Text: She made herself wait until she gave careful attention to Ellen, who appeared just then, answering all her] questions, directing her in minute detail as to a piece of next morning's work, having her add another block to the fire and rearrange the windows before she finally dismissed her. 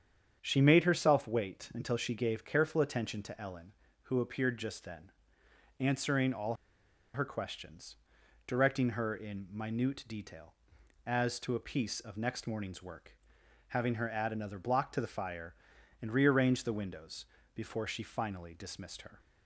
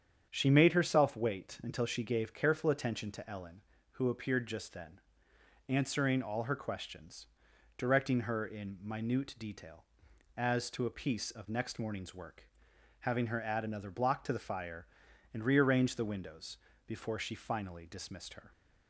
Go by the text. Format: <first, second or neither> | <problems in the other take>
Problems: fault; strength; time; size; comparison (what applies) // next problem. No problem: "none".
second | starts louder than the rest; strong; until 1.4 s; 8 dB; strong in the second // pauses between "all" and "her"; noticeable; at 6.5 s; 0.58 s long // pauses between "windows" and "before"; slight; at 17.2 s; 0.28 s long; slight in the second